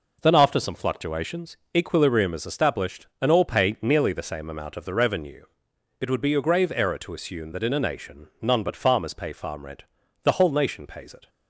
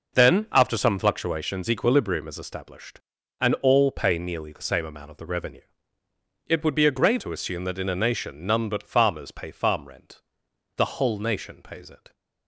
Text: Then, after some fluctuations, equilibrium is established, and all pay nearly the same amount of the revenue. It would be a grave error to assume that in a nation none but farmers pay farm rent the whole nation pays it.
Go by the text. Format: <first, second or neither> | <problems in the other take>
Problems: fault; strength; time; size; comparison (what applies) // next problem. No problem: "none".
first | skips "error"; at 7.2 s // pauses between "rent" and "the"; noticeable; at 10.1 s; 0.56 s long; also in the first